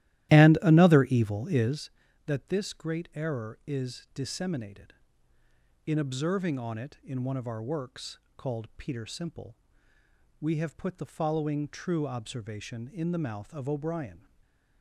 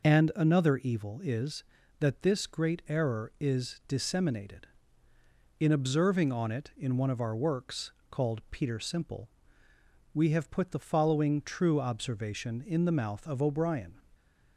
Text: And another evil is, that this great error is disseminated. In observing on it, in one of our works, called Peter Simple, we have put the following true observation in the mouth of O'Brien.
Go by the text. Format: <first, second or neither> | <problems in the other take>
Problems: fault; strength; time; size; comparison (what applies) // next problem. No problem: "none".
second | starts louder than the rest; strong; until 1.9 s; 14.5 dB // stays silent after the last word; slight; from 14.1 s on; 0.7 s long